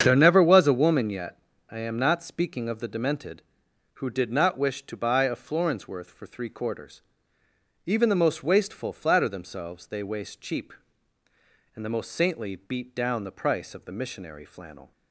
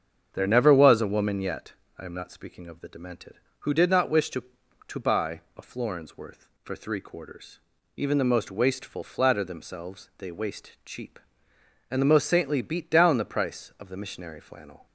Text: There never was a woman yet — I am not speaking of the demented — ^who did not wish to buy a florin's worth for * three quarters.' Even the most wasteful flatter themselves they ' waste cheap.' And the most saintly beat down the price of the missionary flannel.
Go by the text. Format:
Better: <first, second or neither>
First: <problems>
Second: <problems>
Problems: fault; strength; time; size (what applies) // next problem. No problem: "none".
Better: first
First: starts louder than the rest; strong; until 1.0 s; 7.5 dB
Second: starts louder than the rest; strong; until 1.3 s; 7 dB // says "to" twice; at 4.8 s